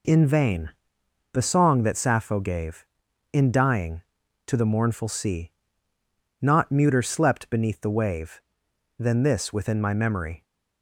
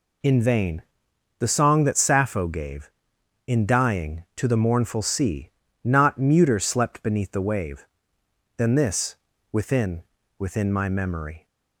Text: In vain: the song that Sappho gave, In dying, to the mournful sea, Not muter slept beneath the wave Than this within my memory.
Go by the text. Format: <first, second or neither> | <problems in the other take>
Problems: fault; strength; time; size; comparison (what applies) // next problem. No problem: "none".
first | pauses between "this" and "within"; at 9.1 s; 0.38 s long // says "within" twice; at 10.3 s